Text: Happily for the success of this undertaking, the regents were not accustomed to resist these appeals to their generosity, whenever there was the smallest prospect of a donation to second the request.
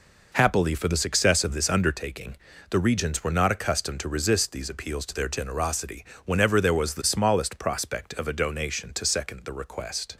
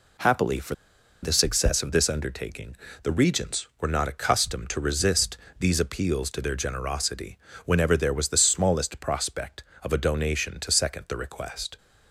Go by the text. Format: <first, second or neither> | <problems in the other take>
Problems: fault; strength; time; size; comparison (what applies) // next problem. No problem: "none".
first | pauses between "for" and "the"; noticeable; at 0.7 s; 0.49 s long // pauses between "resist" and "these"; slight; at 5.3 s; 0.22 s long